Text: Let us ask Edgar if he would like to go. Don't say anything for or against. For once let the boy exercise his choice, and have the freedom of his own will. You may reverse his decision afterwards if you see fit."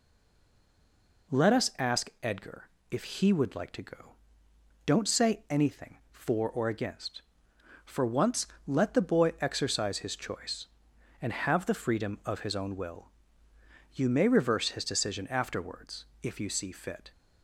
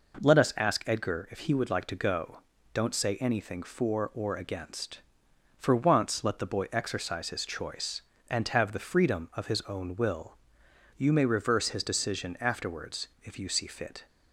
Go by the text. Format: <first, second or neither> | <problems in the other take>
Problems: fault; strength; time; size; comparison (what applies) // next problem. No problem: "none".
second | stays silent before the first word; noticeable; until 1.2 s; 1.2 s long // pauses between "Edgar" and "if"; slight; at 2.6 s; 0.20 s long // pauses between "once" and "let"; slight; at 8.4 s; 0.18 s long // pauses between "afterwards" and "if"; slight; at 16.0 s; 0.18 s long; slight in the second